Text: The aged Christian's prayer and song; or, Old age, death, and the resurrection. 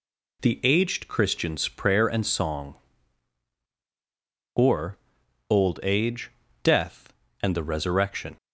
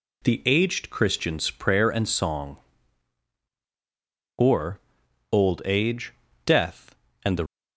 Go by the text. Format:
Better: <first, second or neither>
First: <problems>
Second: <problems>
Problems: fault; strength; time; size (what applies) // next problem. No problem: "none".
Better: first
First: none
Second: stops before "resurrection"; at 7.4 s